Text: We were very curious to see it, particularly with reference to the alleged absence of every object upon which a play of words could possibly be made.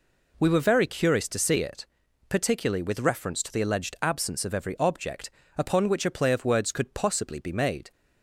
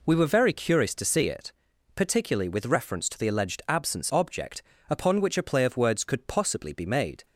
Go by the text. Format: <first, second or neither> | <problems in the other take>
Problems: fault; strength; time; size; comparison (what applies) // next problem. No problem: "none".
first | skips "of every"; at 4.1 s // pauses between "object" and "upon"; slight; at 4.6 s; 0.28 s long; slight in the first